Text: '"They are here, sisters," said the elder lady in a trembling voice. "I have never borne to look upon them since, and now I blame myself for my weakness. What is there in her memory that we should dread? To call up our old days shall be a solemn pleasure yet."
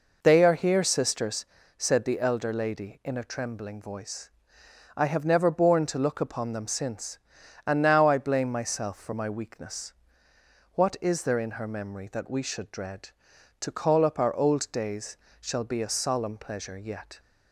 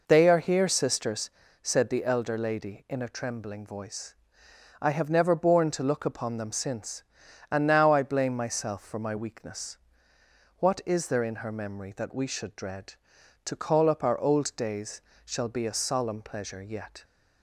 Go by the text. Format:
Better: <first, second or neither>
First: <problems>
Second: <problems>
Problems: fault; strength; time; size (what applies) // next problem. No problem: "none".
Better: neither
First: pauses between "days" and "shall"; slight; at 15.1 s; 0.22 s long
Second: pauses between "days" and "shall"; slight; at 15.0 s; 0.22 s long